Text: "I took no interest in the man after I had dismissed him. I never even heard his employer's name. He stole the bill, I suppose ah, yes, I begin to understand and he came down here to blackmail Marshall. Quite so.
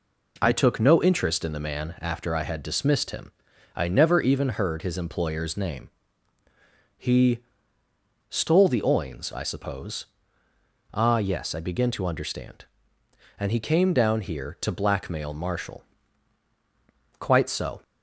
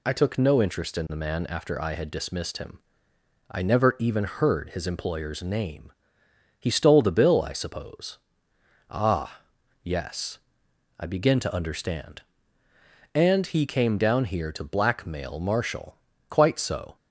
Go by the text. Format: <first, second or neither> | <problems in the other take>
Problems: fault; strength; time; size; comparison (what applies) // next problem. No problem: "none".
second | pauses between "He" and "stole"; noticeable; at 7.4 s; 0.85 s long // says "oins" for "bill"; at 8.8 s // pauses between "suppose" and "ah"; noticeable; at 10.0 s; 0.86 s long; noticeable in the second